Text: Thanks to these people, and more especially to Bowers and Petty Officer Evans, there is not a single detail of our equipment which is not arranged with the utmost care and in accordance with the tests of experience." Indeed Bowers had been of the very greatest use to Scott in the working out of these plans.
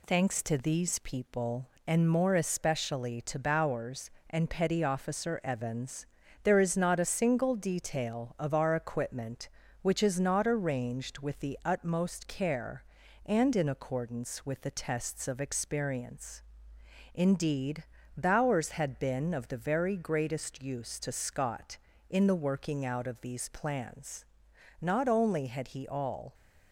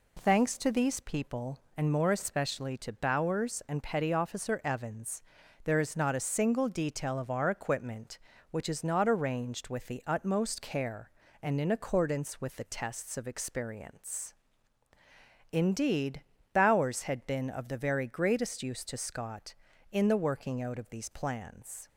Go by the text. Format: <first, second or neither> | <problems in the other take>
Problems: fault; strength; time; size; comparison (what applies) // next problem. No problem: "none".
second | pauses between "Indeed" and "Bowers"; slight; at 17.8 s; 0.34 s long; slight in the second // goes on to say "Not only had he all"; from 24.8 s on; 1.5 s long